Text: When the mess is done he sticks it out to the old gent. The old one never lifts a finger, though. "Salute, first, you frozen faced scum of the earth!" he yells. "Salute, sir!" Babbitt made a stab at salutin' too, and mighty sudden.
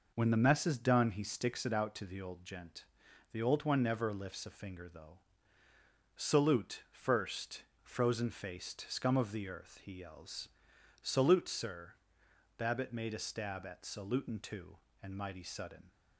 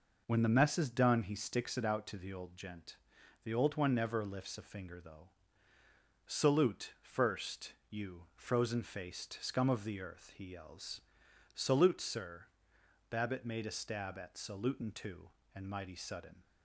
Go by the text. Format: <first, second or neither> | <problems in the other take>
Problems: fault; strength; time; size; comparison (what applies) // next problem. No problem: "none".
second | skips "you"; at 7.7 s